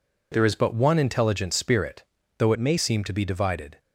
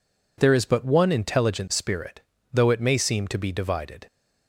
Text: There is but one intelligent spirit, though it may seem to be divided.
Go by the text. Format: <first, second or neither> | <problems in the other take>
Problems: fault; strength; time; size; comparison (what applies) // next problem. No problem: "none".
second | changes voice from "it" to "may"; from 2.5 to 2.7 s; 0.2 s long